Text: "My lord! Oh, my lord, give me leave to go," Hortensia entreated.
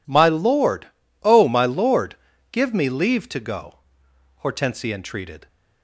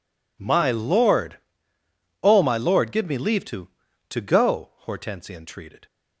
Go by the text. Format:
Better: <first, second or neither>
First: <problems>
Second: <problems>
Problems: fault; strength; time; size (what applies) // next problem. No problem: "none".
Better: first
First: none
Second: says "to" twice; at 4.0 s